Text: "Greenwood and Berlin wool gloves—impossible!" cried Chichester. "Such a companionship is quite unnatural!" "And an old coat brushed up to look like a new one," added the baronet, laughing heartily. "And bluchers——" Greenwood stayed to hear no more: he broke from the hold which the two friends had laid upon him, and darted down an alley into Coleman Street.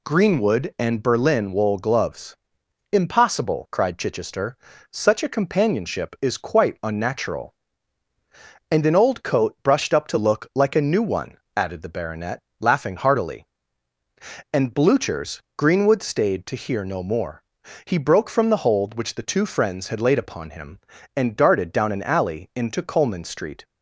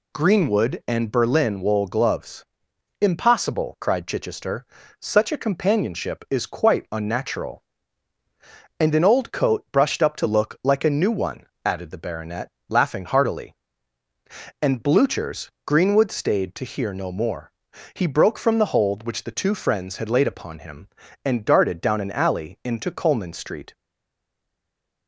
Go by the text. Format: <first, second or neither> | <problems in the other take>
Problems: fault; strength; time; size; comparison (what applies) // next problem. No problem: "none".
first | stays silent after the last word; noticeable; from 23.7 s on; 1.3 s long